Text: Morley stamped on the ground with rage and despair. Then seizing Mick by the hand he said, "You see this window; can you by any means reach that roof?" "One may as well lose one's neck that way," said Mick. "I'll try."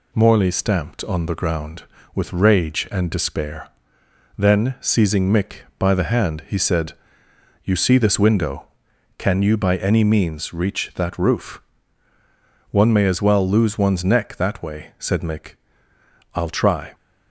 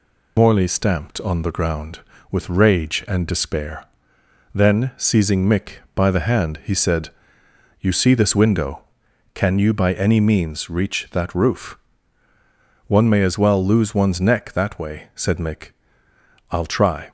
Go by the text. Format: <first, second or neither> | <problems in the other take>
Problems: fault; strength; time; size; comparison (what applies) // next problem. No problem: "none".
first | loses the start of "Morley"; at 0.3 s; 65 ms